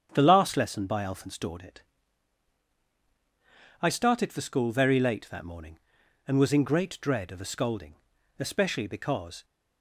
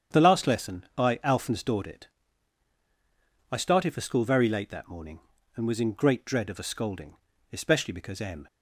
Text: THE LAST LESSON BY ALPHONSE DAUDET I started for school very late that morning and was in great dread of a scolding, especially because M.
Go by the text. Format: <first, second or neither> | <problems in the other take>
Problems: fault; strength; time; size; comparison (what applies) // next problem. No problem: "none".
second | starts louder than the rest; strong; until 1.1 s; 8.5 dB; strong in the second // pauses between "DAUDET" and "I"; strong; at 1.8 s; 1.9 s long; strong in the second // stops before "M"; at 9.4 s